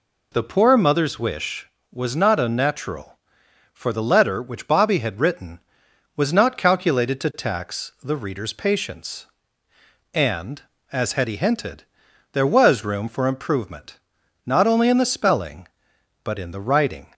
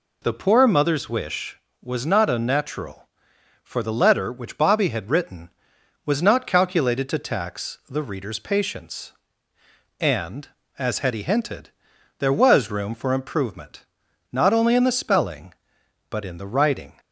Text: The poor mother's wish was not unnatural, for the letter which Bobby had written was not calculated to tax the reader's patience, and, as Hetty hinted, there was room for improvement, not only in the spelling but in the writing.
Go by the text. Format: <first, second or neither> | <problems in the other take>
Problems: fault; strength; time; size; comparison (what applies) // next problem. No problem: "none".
neither | none